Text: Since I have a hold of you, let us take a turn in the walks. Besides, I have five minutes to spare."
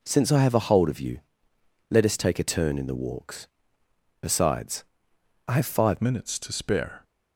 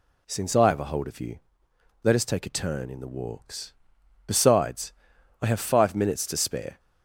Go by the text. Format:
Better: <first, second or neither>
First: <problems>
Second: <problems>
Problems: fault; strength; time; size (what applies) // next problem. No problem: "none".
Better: second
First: changes voice at "minutes"; from 6.0 s on; 1.0 s long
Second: none